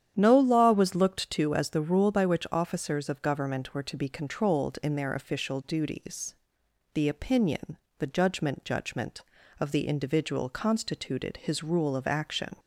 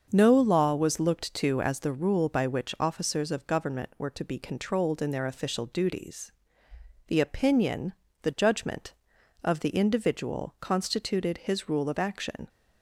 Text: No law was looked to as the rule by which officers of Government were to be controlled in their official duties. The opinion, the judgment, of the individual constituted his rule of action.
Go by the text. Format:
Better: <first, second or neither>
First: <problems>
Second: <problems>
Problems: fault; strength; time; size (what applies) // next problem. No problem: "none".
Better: second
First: starts louder than the rest; strong; until 1.1 s; 9.5 dB // says "judgment" twice; at 8.6 s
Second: starts louder than the rest; until 1.1 s; 6.5 dB